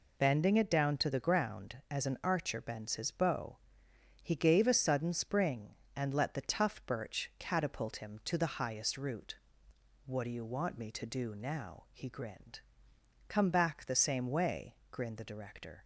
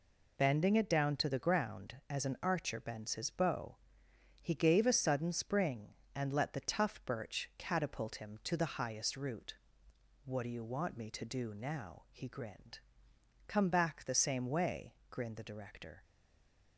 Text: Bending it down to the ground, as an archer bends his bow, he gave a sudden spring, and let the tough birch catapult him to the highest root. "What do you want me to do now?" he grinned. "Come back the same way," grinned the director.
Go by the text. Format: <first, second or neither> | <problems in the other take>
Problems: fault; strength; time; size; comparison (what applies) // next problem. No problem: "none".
first | stays silent after the last word; slight; from 16.0 s on; 0.7 s long